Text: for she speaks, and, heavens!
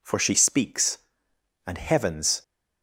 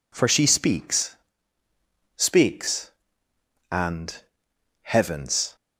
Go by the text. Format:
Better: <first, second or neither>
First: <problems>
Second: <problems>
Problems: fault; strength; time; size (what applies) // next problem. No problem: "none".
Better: first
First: none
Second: says "speaks" twice; at 2.1 s